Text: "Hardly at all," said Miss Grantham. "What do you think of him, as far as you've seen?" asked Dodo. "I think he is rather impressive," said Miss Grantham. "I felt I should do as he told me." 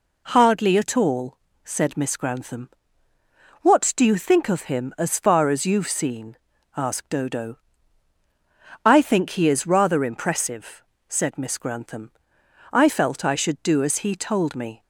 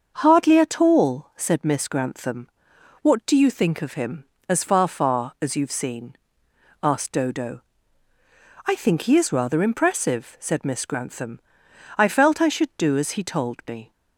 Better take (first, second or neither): first